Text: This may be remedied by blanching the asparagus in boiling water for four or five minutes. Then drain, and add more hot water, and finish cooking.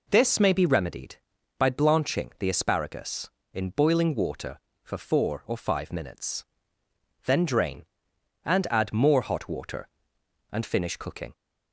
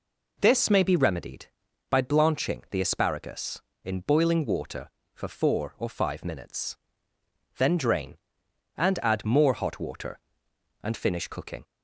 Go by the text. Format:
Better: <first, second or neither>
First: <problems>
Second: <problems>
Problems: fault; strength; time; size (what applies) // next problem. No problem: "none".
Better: neither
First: none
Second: none